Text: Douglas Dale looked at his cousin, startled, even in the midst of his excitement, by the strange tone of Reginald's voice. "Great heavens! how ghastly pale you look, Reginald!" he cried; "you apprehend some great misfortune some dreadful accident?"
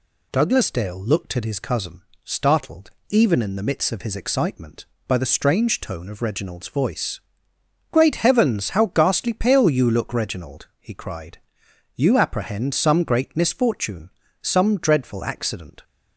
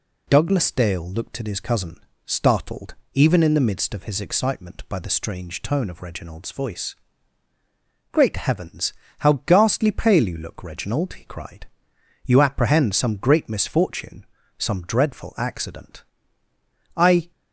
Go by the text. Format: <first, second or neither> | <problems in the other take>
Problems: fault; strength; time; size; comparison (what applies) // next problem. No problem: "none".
first | pauses between "misfortune" and "some"; slight; at 14.2 s; 0.32 s long; slight in the first // goes on to say "I"; slight; from 16.9 s on; 0.36 s long